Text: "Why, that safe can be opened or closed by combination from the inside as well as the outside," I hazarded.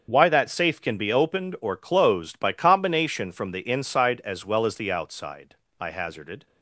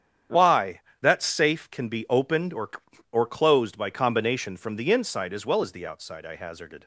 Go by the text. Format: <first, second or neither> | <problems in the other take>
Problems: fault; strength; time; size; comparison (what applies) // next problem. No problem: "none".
first | starts louder than the rest; strong; until 1.5 s; 9 dB; also in the first // says "or" twice; at 3.1 s